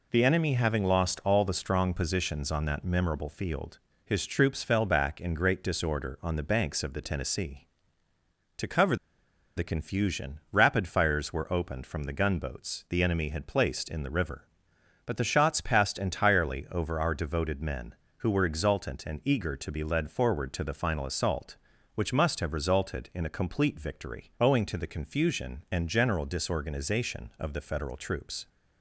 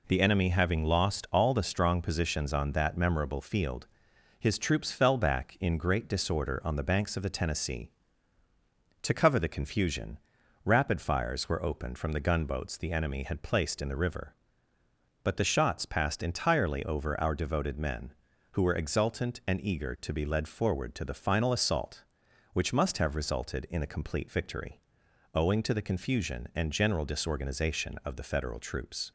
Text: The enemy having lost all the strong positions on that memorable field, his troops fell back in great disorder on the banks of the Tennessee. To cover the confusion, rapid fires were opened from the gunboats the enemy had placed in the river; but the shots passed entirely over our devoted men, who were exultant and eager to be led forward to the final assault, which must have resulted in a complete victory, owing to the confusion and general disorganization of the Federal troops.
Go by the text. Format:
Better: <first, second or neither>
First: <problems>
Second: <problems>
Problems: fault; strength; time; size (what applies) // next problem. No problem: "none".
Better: second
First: pauses between "cover" and "the"; noticeable; at 8.9 s; 0.61 s long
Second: none